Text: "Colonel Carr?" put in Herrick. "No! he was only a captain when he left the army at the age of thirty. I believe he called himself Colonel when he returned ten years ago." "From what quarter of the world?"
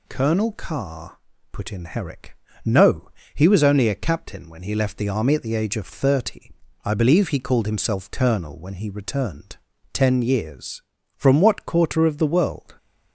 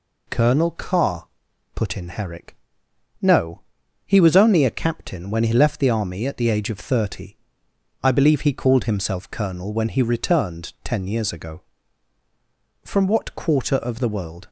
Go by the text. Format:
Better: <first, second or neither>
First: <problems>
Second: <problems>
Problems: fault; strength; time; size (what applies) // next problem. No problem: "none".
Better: second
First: pauses between "returned" and "ten"; at 9.5 s; 0.38 s long // skips "ago"; at 10.9 s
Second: none